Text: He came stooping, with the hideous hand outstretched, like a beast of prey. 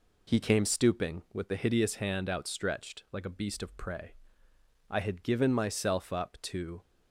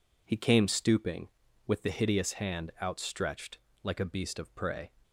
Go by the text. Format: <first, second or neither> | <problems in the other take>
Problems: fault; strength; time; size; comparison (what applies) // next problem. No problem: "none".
second | goes on to say "I had given myself up to"; strong; from 4.9 s on; 1.9 s long